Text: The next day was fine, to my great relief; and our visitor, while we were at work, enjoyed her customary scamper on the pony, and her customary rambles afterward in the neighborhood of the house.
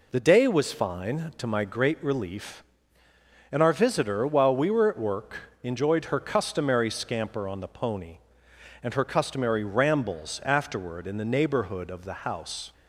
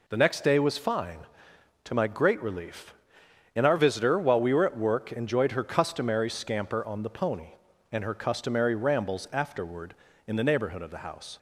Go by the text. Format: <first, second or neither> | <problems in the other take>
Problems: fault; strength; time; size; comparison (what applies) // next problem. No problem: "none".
second | skips "next"; at 0.2 s